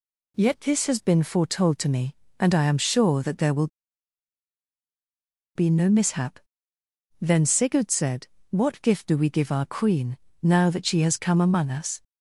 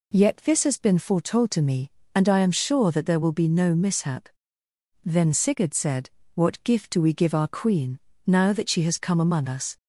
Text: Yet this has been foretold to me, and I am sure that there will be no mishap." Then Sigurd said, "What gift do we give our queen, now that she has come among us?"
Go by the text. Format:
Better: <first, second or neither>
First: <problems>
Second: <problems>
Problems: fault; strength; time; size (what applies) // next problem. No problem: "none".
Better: second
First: pauses between "will" and "be"; strong; at 3.6 s; 1.8 s long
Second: none